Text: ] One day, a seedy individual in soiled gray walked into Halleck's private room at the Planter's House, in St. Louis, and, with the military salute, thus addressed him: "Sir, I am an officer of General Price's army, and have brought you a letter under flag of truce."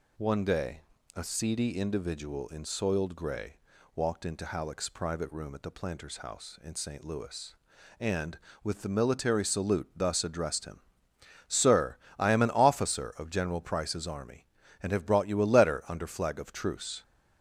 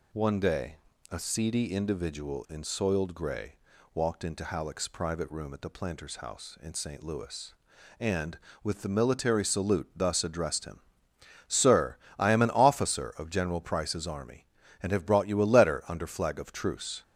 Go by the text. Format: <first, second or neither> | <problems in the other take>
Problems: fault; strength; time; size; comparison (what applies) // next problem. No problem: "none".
neither | pauses between "gray" and "walked"; slight; the same in both